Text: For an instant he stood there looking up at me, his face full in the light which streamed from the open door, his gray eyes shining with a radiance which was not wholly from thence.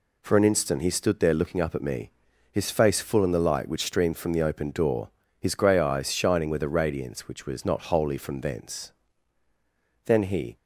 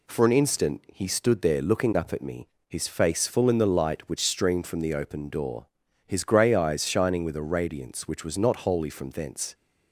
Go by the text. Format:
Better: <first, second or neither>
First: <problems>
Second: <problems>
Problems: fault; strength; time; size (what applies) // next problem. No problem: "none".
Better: second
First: goes on to say "Then he"; from 10.0 s on; 0.50 s long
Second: none